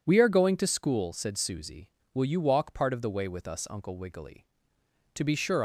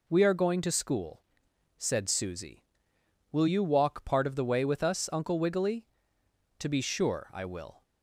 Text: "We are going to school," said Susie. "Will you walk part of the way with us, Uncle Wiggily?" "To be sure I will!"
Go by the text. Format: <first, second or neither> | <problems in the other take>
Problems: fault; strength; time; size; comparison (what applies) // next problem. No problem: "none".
second | stops before "I will"; at 5.5 s